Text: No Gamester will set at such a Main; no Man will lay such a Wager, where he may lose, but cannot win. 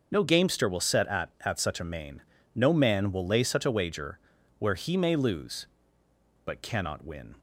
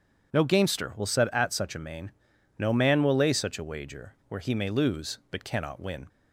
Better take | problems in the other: second | starts louder than the rest; until 1.1 s; 6.5 dB // says "at" twice; at 1.4 s

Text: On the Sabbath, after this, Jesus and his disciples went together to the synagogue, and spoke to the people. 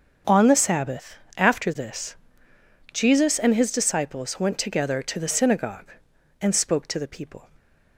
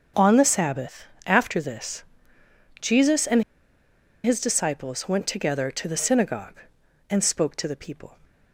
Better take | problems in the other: first | starts louder than the rest; until 1.3 s; 6.5 dB; also in the first // pauses between "and" and "his"; noticeable; at 3.4 s; 0.81 s long

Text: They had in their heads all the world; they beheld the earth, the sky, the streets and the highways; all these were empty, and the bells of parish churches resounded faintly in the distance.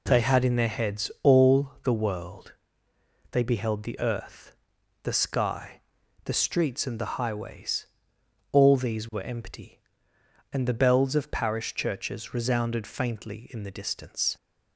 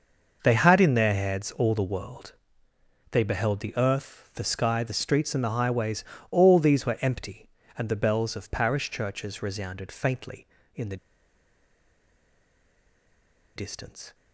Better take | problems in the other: first | starts louder than the rest; noticeable; until 1.4 s; 6 dB // pauses between "the" and "distance"; strong; at 10.9 s; 2.6 s long

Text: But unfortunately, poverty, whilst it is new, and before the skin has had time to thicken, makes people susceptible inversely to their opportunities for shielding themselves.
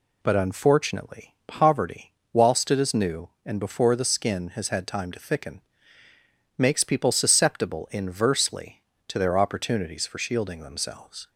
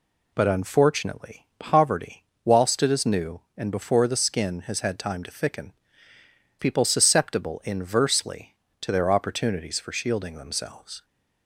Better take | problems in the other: first | skips "makes"; at 6.1 s

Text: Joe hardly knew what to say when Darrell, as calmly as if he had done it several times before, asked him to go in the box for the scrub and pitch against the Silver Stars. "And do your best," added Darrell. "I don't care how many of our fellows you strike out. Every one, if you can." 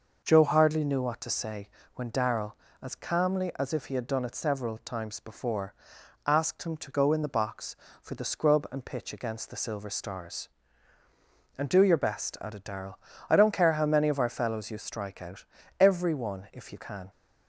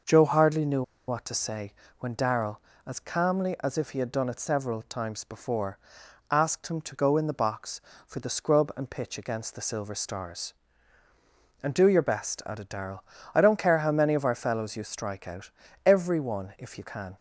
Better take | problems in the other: first | pauses between "knew" and "what"; slight; at 0.8 s; 0.25 s long // pauses between "say" and "when"; slight; at 1.7 s; 0.28 s long; slight in the first

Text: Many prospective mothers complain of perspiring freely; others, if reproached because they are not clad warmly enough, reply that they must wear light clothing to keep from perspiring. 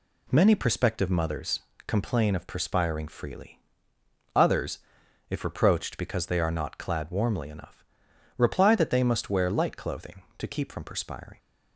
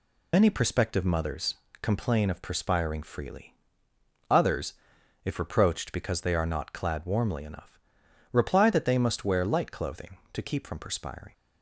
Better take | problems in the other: first | loses the start of "Many"; at 0.3 s; 115 ms // pauses between "mothers" and "complain"; slight; at 1.5 s; 0.26 s long; slight in the first

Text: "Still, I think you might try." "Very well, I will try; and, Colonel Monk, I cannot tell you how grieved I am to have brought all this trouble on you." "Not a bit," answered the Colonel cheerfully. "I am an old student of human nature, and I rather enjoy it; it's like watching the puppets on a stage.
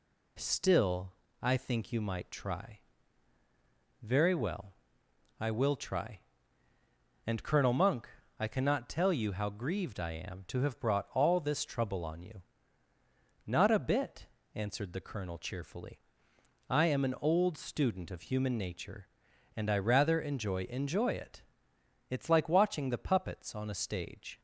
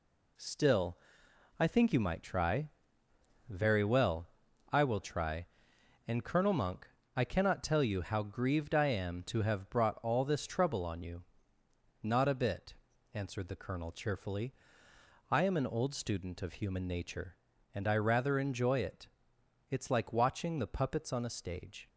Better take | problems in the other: second | says "enjoy" twice; at 20.6 s

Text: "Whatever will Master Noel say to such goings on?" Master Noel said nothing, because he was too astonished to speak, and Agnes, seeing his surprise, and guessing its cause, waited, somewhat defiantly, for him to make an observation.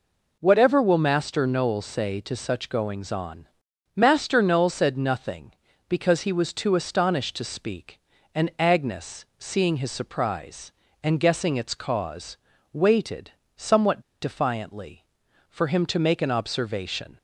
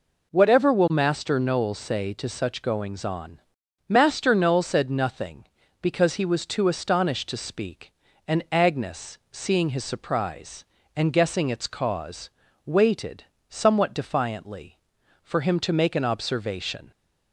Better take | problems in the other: second | pauses between "somewhat" and "defiantly"; slight; at 13.9 s; 0.21 s long

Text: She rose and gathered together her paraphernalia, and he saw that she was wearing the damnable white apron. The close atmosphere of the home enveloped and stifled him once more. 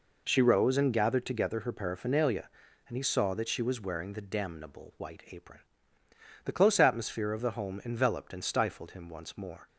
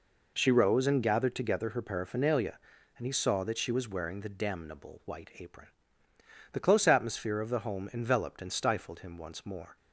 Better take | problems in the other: neither | none

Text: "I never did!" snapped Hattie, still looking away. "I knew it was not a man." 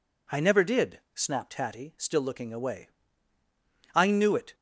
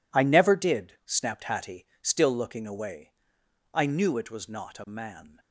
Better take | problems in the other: second | stops before "was not a man"; at 4.5 s

